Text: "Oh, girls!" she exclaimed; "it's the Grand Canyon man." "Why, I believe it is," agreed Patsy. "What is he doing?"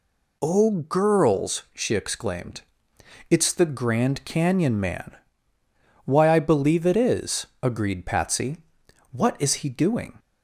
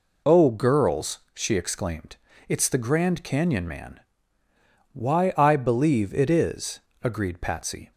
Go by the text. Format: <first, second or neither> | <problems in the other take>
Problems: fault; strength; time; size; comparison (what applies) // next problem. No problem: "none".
first | stops before "What is he doing"; at 7.9 s